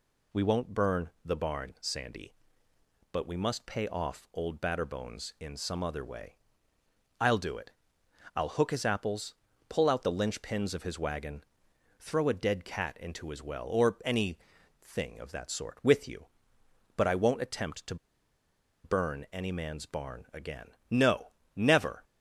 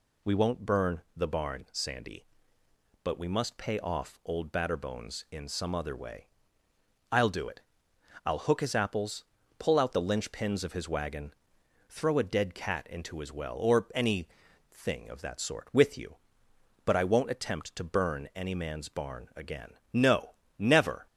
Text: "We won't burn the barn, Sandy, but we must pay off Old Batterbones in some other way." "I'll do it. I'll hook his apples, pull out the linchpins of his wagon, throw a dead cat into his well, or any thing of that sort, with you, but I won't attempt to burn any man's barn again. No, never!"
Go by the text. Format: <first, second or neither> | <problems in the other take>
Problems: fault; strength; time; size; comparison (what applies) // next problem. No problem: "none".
second | pauses between "any" and "thing"; at 14.3 s; 0.44 s long; also in the second // pauses between "to" and "burn"; noticeable; at 17.9 s; 0.88 s long